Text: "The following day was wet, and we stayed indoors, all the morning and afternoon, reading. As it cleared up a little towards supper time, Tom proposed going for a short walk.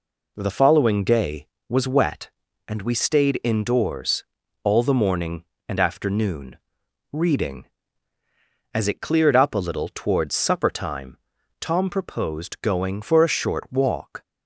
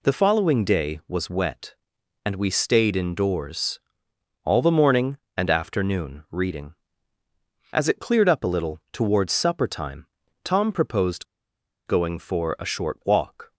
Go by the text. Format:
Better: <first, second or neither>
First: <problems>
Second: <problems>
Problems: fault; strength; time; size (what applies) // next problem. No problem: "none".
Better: first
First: none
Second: pauses between "proposed" and "going"; noticeable; at 11.2 s; 0.62 s long